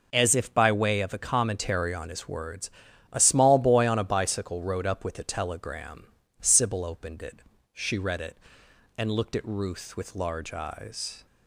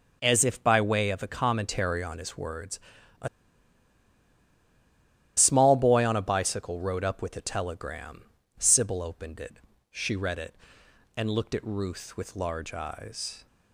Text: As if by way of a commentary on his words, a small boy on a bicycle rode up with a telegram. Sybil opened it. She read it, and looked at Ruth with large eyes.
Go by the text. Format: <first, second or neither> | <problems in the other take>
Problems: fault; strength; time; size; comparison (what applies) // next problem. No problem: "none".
first | pauses between "a" and "small"; strong; at 3.2 s; 2.0 s long